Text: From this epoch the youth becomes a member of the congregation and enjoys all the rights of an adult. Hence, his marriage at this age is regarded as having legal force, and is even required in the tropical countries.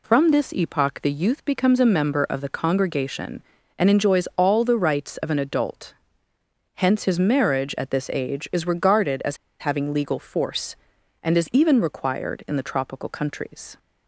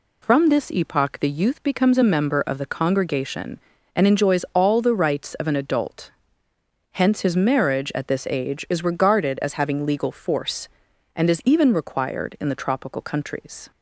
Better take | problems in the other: second | pauses between "as" and "having"; slight; at 9.3 s; 0.23 s long

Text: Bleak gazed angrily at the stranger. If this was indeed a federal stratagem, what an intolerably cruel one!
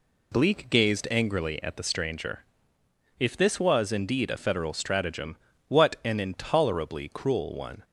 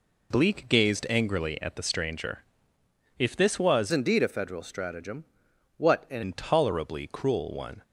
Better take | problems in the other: first | changes voice from "indeed" to "an"; from 3.9 to 6.2 s; 2.3 s long

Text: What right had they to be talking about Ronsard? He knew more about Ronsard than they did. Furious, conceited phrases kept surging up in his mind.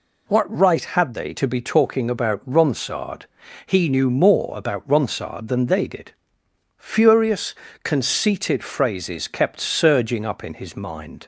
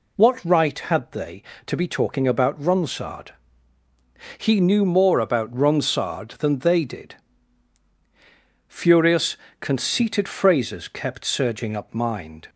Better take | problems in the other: first | skips "in his"; at 11.9 s

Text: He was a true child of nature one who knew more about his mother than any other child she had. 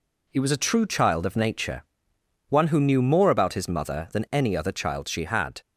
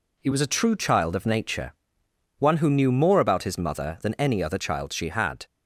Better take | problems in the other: neither | pauses between "nature" and "one"; noticeable; the same in both

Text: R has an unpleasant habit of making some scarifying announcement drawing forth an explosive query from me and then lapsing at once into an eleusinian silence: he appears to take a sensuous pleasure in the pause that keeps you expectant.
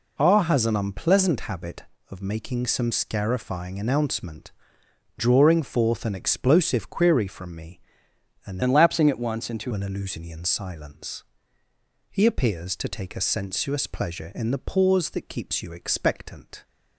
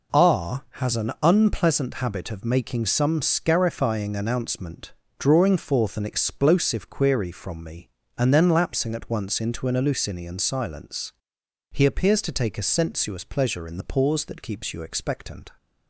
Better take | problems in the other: second | pauses between "announcement" and "drawing"; noticeable; at 4.5 s; 0.66 s long; slight in the second // changes voice from "then" to "into"; from 8.6 to 9.7 s; 1.1 s long

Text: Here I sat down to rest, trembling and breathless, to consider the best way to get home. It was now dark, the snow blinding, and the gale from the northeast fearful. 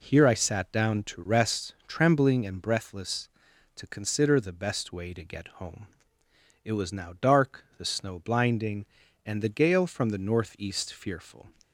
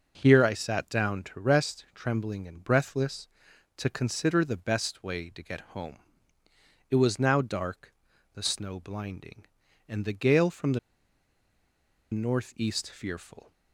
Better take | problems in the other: first | pauses between "the" and "northeast"; strong; at 10.7 s; 1.3 s long

